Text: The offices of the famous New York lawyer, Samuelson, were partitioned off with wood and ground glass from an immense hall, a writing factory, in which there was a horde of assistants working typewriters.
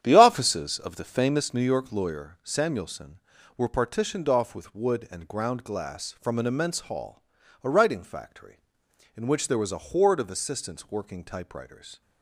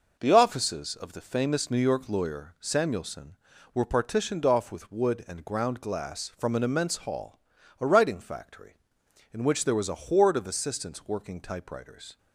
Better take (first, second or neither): second